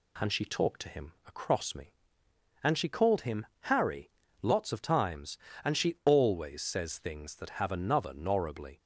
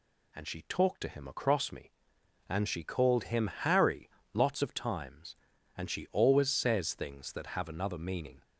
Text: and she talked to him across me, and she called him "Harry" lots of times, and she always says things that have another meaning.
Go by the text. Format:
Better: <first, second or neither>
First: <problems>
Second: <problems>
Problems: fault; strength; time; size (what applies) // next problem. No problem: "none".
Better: second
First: pauses between "him" and "Harry"; slight; at 3.4 s; 0.18 s long // pauses between "Harry" and "lots"; slight; at 4.1 s; 0.30 s long // says "norribly" for "meaning"; at 8.1 s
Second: pauses between "Harry" and "lots"; slight; at 4.0 s; 0.24 s long